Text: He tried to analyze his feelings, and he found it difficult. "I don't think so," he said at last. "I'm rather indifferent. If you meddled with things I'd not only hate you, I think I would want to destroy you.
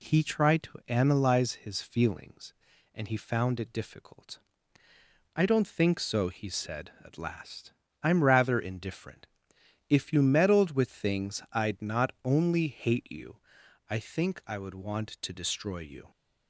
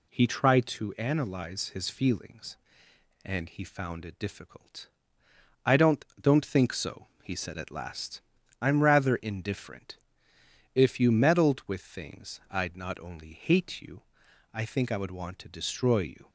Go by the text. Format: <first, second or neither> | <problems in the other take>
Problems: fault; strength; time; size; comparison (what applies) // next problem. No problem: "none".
first | says "don't" twice; at 6.1 s